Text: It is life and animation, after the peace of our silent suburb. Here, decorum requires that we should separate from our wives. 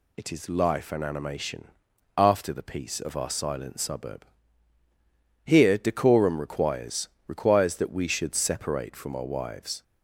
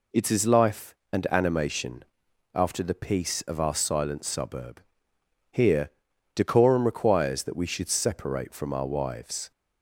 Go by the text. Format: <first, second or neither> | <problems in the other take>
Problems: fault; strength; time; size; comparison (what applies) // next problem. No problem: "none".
second | says "requires" twice; at 7.2 s